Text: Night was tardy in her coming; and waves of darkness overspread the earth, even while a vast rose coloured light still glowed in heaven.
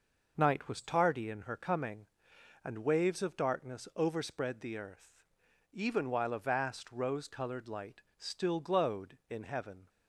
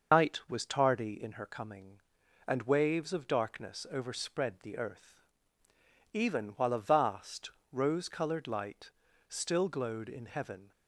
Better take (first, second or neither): first